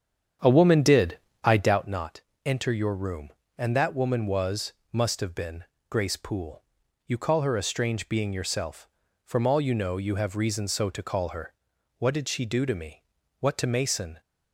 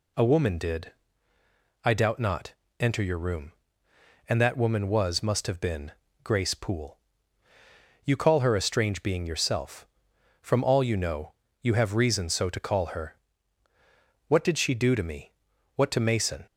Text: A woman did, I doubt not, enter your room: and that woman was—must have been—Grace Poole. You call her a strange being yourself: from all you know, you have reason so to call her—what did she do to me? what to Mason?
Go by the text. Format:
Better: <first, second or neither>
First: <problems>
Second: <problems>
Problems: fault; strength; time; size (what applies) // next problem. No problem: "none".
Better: second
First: starts louder than the rest; strong; until 2.0 s; 8 dB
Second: none